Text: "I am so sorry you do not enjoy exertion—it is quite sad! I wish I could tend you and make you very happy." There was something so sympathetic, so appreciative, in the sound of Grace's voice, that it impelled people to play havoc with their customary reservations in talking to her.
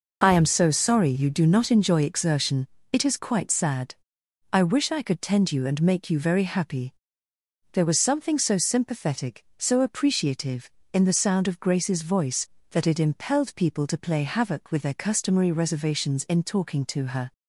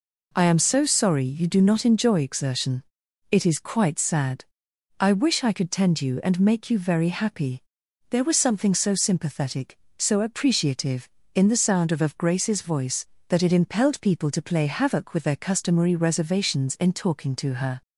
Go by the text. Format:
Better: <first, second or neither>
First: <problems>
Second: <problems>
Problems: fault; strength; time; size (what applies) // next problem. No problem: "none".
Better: first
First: none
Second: says "of" twice; at 11.9 s